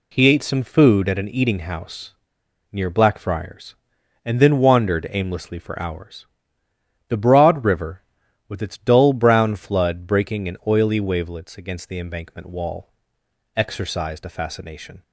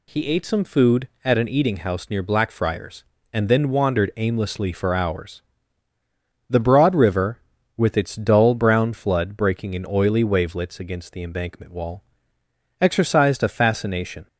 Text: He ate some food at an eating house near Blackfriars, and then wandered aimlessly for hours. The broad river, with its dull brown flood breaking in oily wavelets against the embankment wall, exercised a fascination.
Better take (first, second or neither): second